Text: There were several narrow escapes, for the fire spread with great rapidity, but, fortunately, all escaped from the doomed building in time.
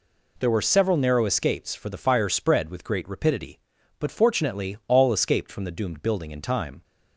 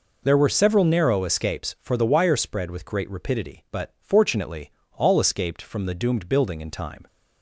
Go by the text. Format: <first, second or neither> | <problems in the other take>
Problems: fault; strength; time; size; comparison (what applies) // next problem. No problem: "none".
first | says "wire" for "fire"; at 2.0 s